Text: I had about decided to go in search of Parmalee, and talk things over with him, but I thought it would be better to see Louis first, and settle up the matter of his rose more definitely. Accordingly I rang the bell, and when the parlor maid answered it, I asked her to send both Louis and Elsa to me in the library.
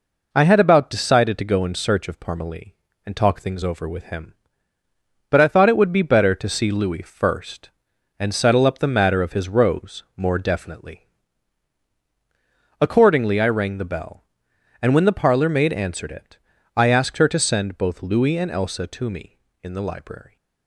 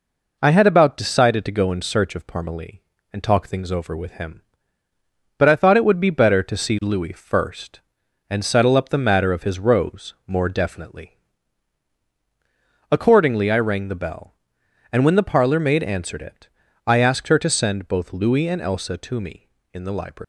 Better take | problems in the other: first | leaves "library" unfinished; at 20.2 s; 215 ms

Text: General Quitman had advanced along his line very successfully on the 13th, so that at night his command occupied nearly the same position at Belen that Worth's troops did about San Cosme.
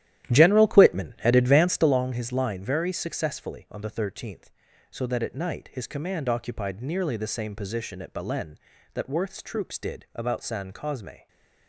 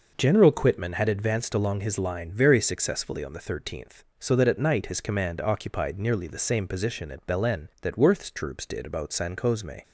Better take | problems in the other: second | starts louder than the rest; strong; until 2.0 s; 12.5 dB // stays silent after the last word; slight; from 11.1 s on; 0.5 s long

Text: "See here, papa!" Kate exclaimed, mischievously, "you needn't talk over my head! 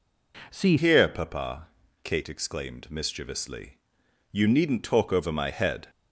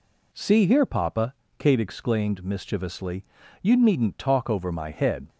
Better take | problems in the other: second | changes voice at "here"; from 0.7 s on; 5.1 s long

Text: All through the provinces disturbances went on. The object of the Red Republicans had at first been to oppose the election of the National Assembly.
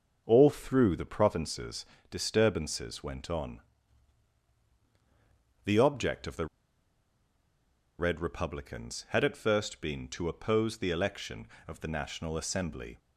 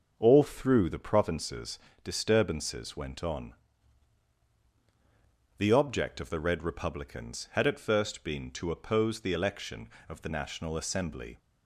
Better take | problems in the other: second | starts louder than the rest; until 1.2 s; 6.5 dB; also in the second // pauses between "provinces" and "disturbances"; slight; at 1.8 s; 0.26 s long; slight in the second // pauses between "the" and "Red"; strong; at 6.4 s; 1.5 s long

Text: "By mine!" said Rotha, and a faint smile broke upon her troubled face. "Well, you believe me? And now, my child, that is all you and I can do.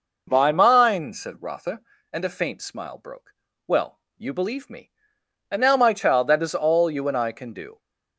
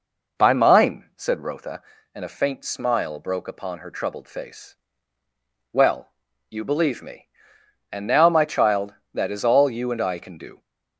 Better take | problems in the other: second | skips "upon her troubled face"; at 3.5 s

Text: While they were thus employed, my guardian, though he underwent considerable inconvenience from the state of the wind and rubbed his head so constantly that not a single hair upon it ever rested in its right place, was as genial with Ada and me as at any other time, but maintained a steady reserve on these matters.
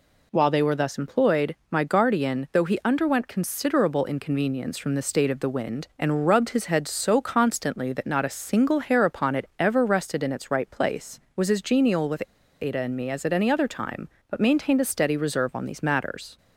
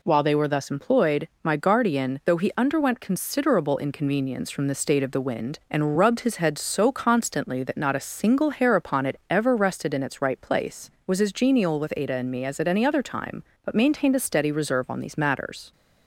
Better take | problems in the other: second | pauses between "with" and "Ada"; at 12.2 s; 0.38 s long

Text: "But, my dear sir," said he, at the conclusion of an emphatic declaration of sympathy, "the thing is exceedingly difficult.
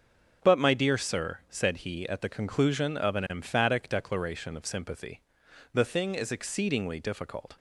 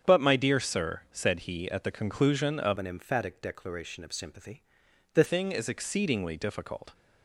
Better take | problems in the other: first | starts louder than the rest; strong; until 1.1 s; 8 dB; also in the first // changes voice from "an" to "the"; from 2.7 to 5.2 s; 2.5 s long

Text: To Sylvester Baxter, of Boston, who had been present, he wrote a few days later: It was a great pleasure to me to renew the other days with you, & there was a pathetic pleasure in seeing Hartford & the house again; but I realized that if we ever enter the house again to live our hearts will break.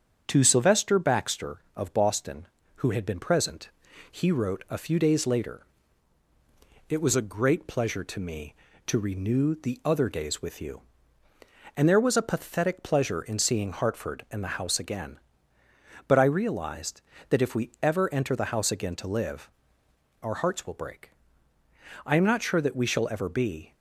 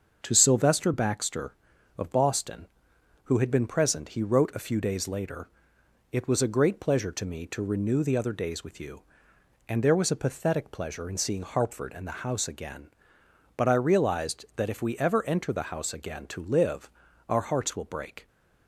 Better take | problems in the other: second | starts louder than the rest; strong; until 1.2 s; 7.5 dB; also in the second // pauses between "live" and "our"; noticeable; at 19.4 s; 0.72 s long; slight in the second // goes on to say "I am not sure that we shall ever be"; strong; from 22.0 s on; 1.6 s long

